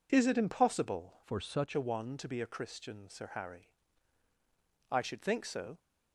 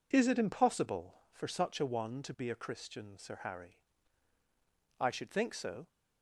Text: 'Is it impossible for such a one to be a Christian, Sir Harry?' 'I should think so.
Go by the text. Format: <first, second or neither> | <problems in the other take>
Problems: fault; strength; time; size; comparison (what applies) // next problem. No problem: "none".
second | changes voice from "for" to "such"; from 1.2 to 1.7 s; 0.5 s long